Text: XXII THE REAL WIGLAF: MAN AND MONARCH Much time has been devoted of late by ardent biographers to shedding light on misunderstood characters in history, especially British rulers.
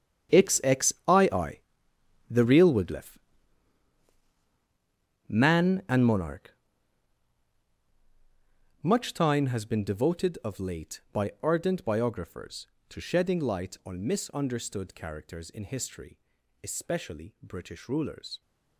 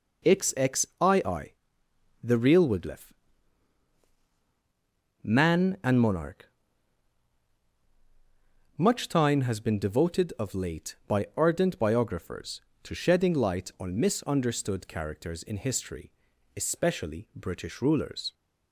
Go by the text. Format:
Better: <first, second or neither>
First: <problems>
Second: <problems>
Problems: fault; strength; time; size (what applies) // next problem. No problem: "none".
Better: second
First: gets quieter; strong; throughout; 13.5 dB // pauses between "XXII" and "THE"; noticeable; at 1.5 s; 0.72 s long // pauses between "MONARCH" and "Much"; strong; at 6.4 s; 2.3 s long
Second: pauses between "XXII" and "THE"; noticeable; at 1.5 s; 0.72 s long // pauses between "MONARCH" and "Much"; strong; at 6.4 s; 2.3 s long